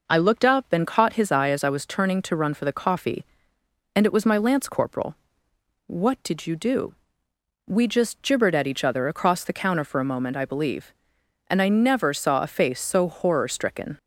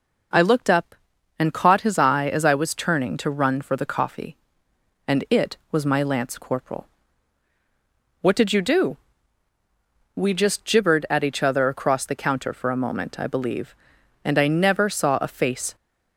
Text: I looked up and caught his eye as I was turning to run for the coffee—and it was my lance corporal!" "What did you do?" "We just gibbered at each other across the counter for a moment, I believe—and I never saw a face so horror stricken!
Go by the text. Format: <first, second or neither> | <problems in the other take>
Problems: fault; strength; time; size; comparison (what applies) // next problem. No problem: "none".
first | stops before "so horror stricken"; at 15.7 s